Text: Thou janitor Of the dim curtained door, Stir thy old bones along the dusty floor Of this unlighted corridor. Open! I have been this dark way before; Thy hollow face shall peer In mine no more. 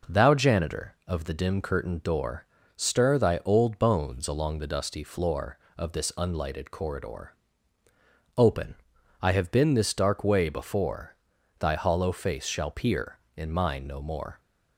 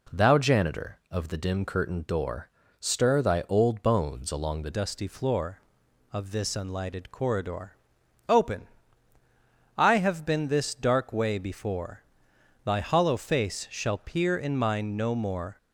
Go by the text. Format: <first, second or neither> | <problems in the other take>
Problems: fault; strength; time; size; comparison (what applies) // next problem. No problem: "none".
first | changes voice at "dusty"; from 4.7 s on; 10.8 s long